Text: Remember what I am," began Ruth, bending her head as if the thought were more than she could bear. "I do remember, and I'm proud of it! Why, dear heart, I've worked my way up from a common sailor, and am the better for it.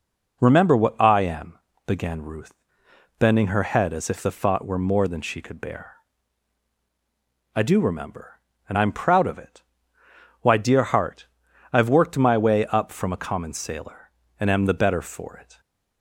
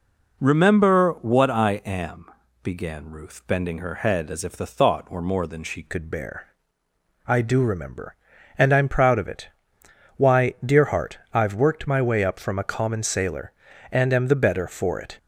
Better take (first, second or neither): first